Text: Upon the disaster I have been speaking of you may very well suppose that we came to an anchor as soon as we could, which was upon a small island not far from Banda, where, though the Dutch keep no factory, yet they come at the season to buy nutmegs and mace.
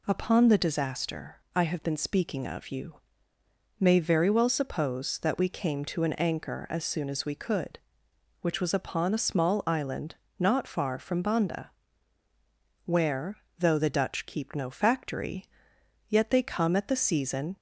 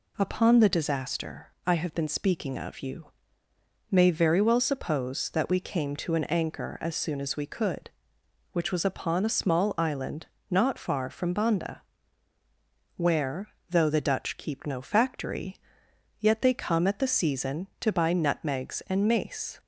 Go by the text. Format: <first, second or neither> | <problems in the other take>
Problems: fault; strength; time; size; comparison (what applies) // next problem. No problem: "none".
second | pauses between "disaster" and "I"; slight; at 1.3 s; 0.20 s long; slight in the second // pauses between "you" and "may"; noticeable; at 2.9 s; 0.84 s long; noticeable in the second // pauses between "island" and "not"; slight; at 10.1 s; 0.24 s long; slight in the second // stops before "to buy nutmegs and mace"; at 17.5 s